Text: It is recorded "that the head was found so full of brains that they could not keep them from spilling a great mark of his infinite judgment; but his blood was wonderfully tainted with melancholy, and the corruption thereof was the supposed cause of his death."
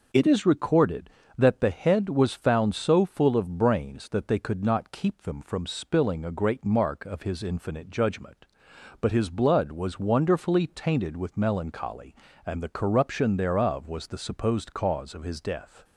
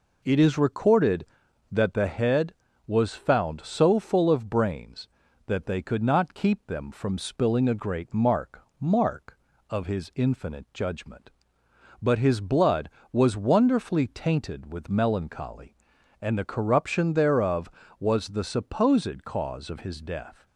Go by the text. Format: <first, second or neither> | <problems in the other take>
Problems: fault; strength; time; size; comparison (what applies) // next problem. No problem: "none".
first | says "mark" twice; at 8.7 s